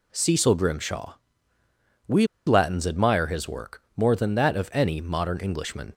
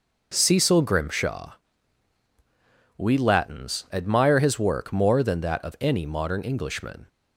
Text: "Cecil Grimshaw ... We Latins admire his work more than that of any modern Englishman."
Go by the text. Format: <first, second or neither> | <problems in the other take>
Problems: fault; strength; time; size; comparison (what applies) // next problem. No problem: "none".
second | pauses between "We" and "Latins"; slight; at 2.2 s; 0.21 s long